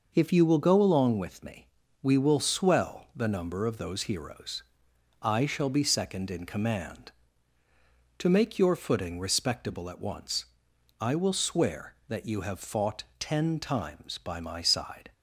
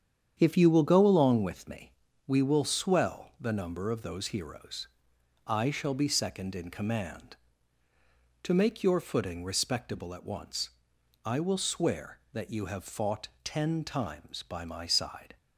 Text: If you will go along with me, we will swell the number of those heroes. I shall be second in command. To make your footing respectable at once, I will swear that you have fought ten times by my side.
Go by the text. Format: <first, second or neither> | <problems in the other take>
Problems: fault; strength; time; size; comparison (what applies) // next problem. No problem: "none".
first | starts louder than the rest; strong; until 2.1 s; 8.5 dB